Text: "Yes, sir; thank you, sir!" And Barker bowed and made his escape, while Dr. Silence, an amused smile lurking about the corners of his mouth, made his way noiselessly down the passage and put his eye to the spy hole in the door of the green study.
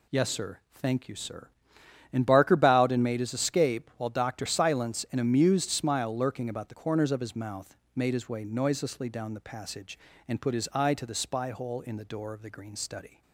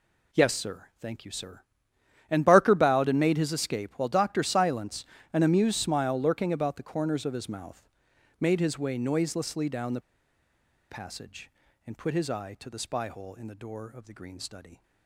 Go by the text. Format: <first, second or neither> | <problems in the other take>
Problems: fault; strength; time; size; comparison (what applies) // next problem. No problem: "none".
first | pauses between "the" and "passage"; noticeable; at 10.0 s; 0.88 s long